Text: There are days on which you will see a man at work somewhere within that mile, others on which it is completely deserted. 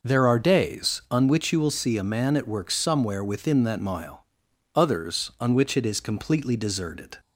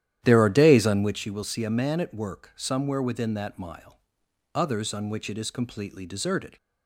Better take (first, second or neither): first